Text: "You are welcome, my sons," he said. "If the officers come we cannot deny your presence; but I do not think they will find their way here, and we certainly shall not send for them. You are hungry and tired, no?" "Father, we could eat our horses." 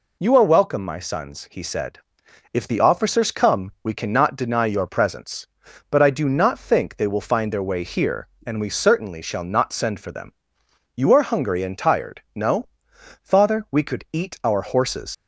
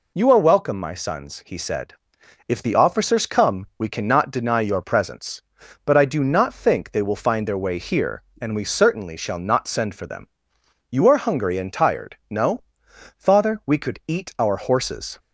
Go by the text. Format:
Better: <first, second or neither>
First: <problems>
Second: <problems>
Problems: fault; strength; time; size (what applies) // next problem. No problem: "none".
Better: second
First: leaves "horses" unfinished; at 15.1 s; 90 ms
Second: none